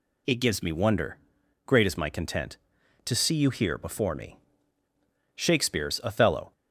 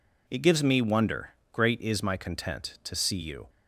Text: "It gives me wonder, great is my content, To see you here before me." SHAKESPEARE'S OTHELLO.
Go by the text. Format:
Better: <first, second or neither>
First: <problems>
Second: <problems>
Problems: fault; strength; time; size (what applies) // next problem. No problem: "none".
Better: first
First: none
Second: stops before "here before me SHAKESPEARE'S OTHELLO"; at 3.4 s